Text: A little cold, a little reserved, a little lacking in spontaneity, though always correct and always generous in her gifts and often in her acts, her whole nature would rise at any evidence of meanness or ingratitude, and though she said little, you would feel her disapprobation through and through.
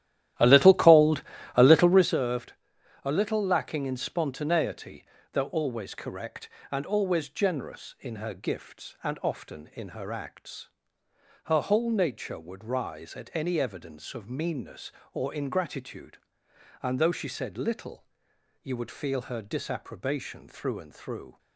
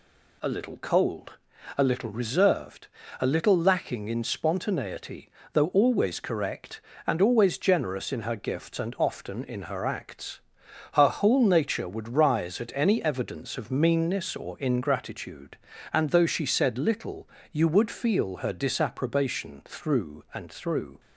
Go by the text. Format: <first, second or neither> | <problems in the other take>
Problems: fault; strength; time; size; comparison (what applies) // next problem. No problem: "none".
second | starts louder than the rest; strong; until 2.2 s; 13 dB